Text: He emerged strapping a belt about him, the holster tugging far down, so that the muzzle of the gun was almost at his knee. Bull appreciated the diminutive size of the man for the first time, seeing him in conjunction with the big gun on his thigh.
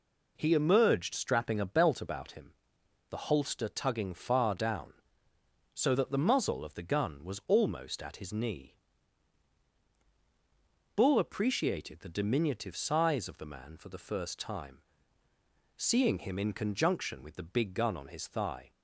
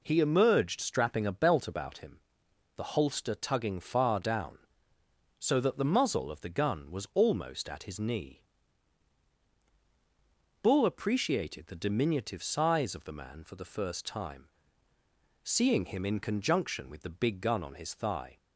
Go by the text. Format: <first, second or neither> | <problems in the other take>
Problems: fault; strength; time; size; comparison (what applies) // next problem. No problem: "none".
neither | none